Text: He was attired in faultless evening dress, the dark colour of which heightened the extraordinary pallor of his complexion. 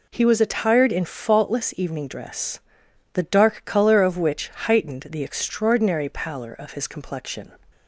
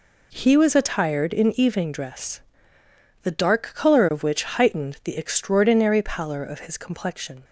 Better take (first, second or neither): first